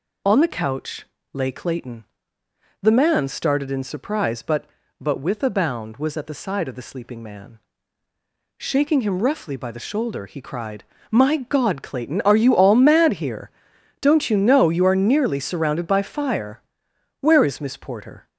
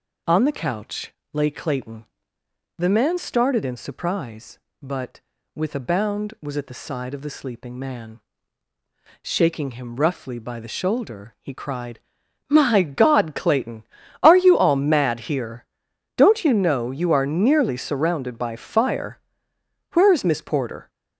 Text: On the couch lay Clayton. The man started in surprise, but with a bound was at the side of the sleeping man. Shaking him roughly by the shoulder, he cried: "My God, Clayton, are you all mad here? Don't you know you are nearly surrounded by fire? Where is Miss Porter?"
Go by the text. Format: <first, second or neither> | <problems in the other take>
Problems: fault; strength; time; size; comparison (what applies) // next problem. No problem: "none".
second | pauses between "couch" and "lay"; slight; at 1.0 s; 0.30 s long; slight in the second // says "but" twice; at 4.9 s